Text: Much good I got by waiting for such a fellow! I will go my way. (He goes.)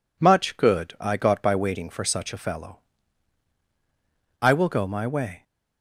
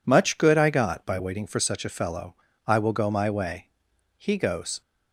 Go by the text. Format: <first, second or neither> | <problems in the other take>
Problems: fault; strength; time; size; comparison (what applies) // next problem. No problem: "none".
second | stops before "He goes"; at 5.4 s